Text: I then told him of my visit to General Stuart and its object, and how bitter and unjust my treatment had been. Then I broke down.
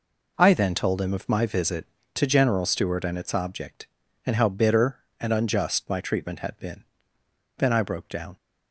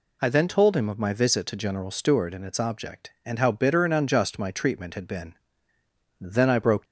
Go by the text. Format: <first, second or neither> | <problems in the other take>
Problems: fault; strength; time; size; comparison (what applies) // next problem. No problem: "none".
first | stops before "down"; at 6.8 s